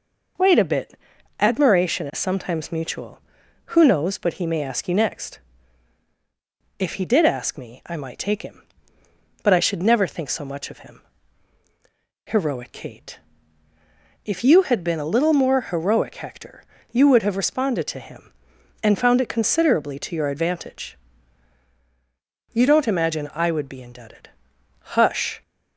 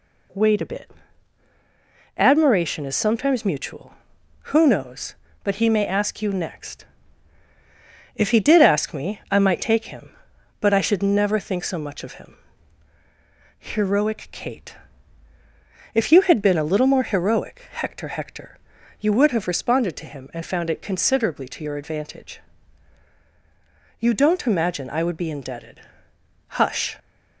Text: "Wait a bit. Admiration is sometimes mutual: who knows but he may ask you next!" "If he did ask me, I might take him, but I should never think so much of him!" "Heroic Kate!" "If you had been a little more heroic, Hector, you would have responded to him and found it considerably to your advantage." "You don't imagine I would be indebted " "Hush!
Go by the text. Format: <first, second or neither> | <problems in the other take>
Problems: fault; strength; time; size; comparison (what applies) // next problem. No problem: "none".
first | says "Hector" twice; at 18.0 s